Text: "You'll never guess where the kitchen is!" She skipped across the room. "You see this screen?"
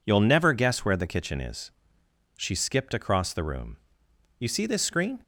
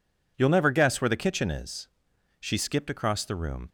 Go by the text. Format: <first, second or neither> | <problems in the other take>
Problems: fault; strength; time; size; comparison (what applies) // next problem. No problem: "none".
first | stops before "You see this screen"; at 3.6 s